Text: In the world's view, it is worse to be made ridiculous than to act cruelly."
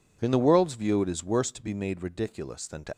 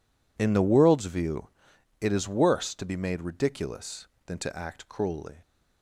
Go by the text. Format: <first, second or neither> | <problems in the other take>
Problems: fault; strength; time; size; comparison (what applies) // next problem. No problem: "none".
second | stops before "act cruelly"; at 2.9 s